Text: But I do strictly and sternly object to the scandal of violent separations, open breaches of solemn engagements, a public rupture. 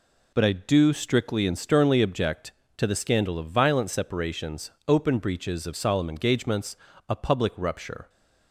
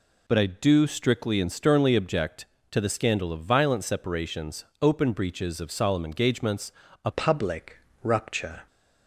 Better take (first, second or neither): first